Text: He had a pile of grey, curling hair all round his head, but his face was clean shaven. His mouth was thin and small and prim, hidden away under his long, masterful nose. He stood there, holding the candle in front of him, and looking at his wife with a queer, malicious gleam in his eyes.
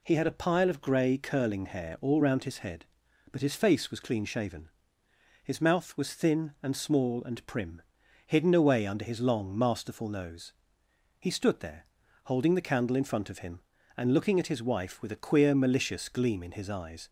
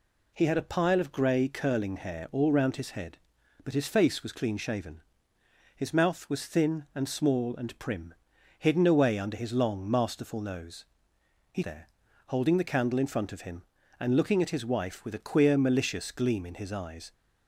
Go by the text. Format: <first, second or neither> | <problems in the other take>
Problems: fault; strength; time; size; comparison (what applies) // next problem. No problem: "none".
first | skips "stood"; at 11.6 s